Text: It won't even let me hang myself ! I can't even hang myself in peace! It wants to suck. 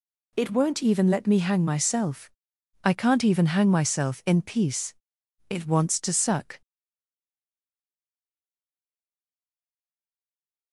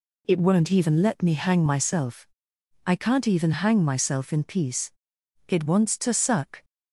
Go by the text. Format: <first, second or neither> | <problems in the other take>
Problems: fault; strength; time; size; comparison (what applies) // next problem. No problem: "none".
second | stays silent after the last word; strong; from 6.6 s on; 4.1 s long